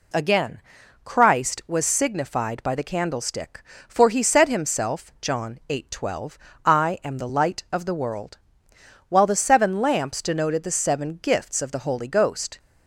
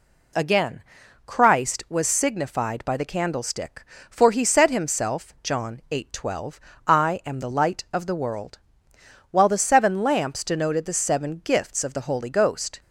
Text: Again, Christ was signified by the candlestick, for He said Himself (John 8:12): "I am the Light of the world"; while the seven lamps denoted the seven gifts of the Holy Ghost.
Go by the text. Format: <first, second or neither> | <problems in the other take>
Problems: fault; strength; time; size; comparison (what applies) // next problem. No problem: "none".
neither | none